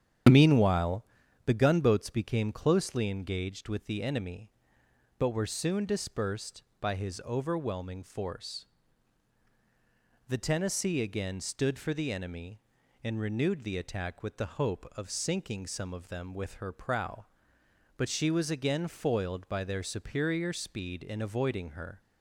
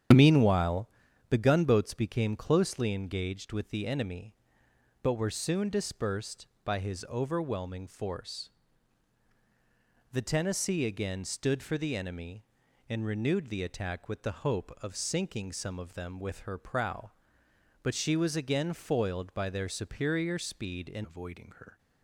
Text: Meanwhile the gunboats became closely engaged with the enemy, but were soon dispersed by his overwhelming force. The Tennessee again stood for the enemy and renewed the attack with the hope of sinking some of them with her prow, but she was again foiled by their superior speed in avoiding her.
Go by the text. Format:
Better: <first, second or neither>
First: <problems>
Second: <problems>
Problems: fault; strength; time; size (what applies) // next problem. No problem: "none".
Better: first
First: starts louder than the rest; strong; until 1.6 s; 9 dB // pauses between "Meanwhile" and "the"; at 1.0 s; 0.40 s long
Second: starts louder than the rest; strong; until 1.5 s; 9 dB // pauses between "Meanwhile" and "the"; at 0.8 s; 0.40 s long // changes voice at "avoiding"; from 21.0 s on; 0.7 s long